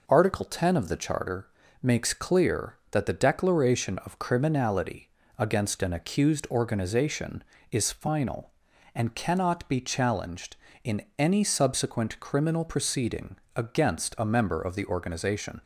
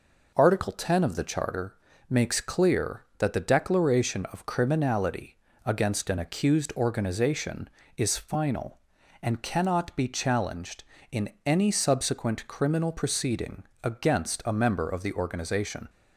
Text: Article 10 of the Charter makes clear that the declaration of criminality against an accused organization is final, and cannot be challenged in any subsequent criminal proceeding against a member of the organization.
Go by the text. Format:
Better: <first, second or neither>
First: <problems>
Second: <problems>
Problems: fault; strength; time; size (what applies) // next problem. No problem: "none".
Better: neither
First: pauses between "Charter" and "makes"; slight; at 1.4 s; 0.34 s long // pauses between "criminality" and "against"; slight; at 5.0 s; 0.26 s long // pauses between "in" and "any"; slight; at 11.0 s; 0.18 s long // pauses between "proceeding" and "against"; slight; at 13.3 s; 0.20 s long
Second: pauses between "Charter" and "makes"; slight; at 1.7 s; 0.34 s long // pauses between "criminality" and "against"; slight; at 5.3 s; 0.26 s long // pauses between "in" and "any"; slight; at 11.2 s; 0.18 s long // pauses between "proceeding" and "against"; slight; at 13.6 s; 0.20 s long